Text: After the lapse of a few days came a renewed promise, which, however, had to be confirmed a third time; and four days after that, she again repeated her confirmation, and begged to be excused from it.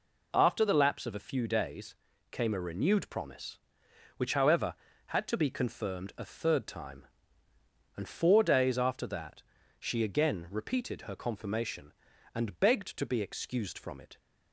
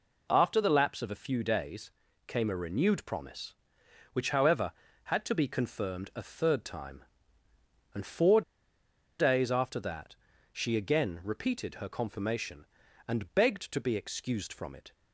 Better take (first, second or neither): first